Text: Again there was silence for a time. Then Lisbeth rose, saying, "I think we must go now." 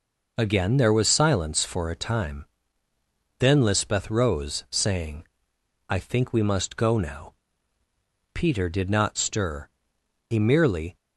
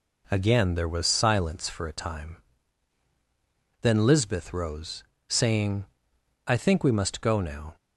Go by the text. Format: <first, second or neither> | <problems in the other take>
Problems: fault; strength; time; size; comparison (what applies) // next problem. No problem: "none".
second | goes on to say "Peter did not stir He merely"; strong; from 8.3 s on; 2.6 s long